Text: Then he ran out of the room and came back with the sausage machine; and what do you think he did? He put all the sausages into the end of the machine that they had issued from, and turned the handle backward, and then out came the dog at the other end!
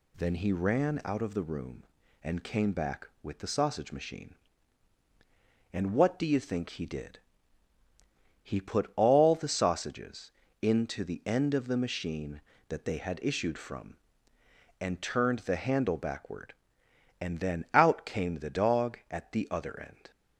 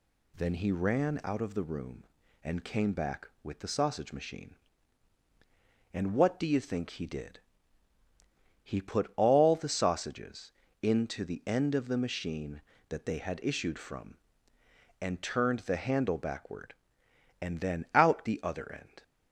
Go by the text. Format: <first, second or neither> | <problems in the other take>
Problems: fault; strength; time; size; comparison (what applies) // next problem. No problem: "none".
first | pauses between "sausages" and "into"; slight; at 10.5 s; 0.32 s long; slight in the first // skips "came the dog at"; at 18.2 s